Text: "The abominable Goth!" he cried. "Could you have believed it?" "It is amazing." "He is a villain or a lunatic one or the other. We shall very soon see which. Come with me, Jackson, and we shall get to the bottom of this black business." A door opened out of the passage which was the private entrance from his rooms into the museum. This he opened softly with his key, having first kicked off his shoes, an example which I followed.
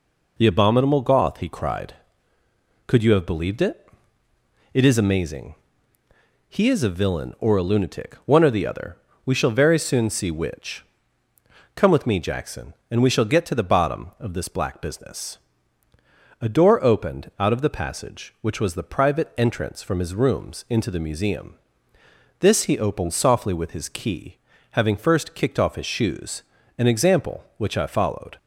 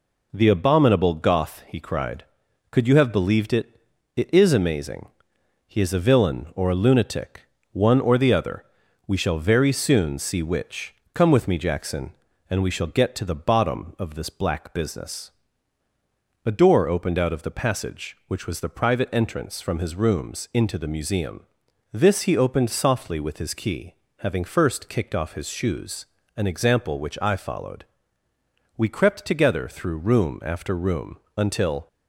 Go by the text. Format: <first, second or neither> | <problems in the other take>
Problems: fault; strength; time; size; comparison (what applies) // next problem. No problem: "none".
first | pauses between "lunatic" and "one"; slight; at 7.4 s; 0.26 s long // goes on to say "We crept together through room after room until"; strong; from 28.7 s on; 3.1 s long